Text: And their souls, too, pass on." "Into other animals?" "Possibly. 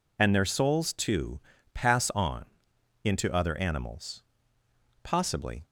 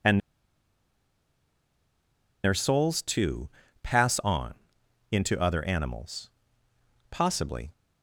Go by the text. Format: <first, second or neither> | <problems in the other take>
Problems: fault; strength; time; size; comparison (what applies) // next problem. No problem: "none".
first | pauses between "And" and "their"; strong; at 0.2 s; 2.2 s long